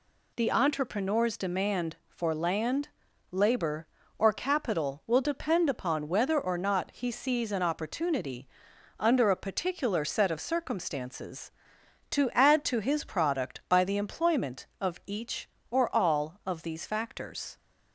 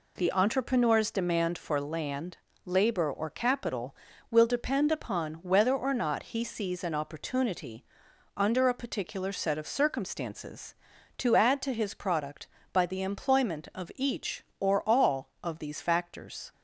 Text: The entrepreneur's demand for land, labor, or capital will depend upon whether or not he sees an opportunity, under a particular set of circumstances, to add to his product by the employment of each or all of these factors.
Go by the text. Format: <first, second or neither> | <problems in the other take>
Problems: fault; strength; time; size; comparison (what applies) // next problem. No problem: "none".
neither | none